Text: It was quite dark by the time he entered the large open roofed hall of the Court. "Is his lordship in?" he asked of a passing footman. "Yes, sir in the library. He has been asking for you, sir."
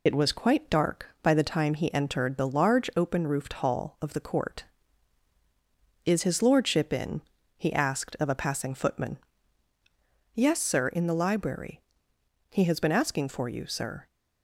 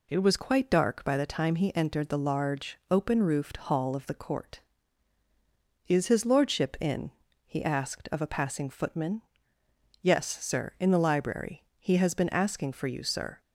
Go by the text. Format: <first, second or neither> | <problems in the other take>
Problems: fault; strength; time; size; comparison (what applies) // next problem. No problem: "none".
second | loses the start of "It"; at 0.0 s; 75 ms